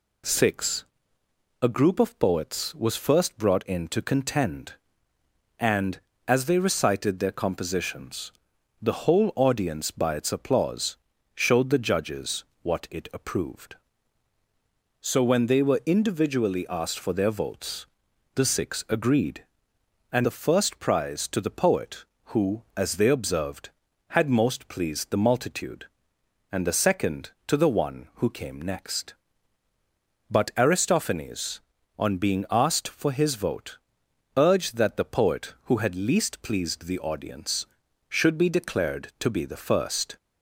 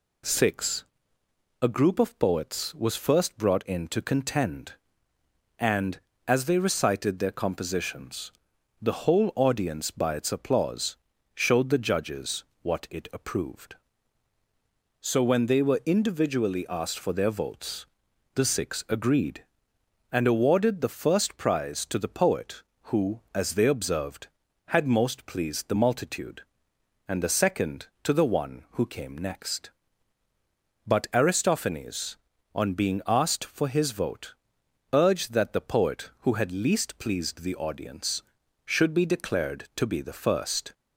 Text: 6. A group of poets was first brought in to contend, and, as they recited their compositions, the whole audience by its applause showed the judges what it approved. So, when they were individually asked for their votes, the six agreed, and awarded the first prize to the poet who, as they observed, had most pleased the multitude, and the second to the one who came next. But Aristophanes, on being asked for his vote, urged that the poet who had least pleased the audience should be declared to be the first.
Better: second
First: pauses between "applause" and "showed"; at 10.9 s; 0.38 s long // pauses between "judges" and "what"; slight; at 12.4 s; 0.20 s long // skips "awarded"; at 20.2 s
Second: pauses between "applause" and "showed"; at 10.9 s; 0.38 s long // pauses between "judges" and "what"; slight; at 12.4 s; 0.20 s long

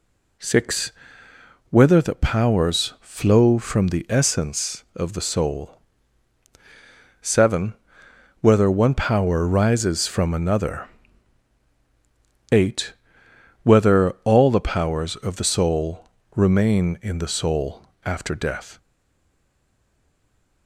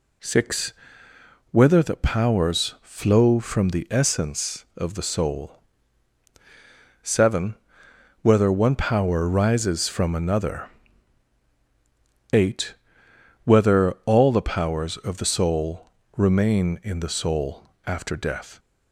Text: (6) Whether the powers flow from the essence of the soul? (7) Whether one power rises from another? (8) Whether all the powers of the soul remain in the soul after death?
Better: second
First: pauses between "soul" and "remain"; slight; at 16.0 s; 0.28 s long // pauses between "soul" and "after"; slight; at 17.8 s; 0.24 s long // stays silent after the last word; noticeable; from 18.7 s on; 1.9 s long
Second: pauses between "soul" and "remain"; slight; at 15.8 s; 0.28 s long // pauses between "soul" and "after"; slight; at 17.6 s; 0.24 s long

